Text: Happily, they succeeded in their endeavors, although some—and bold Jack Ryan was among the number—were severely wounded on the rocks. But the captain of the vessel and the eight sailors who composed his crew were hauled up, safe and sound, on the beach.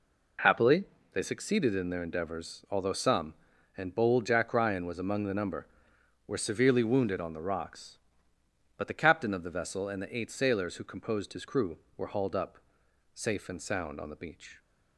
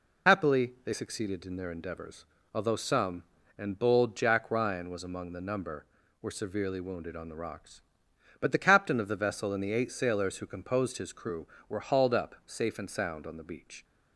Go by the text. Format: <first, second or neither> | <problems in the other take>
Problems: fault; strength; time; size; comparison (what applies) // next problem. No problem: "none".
first | loses the start of "Happily"; at 0.2 s; 45 ms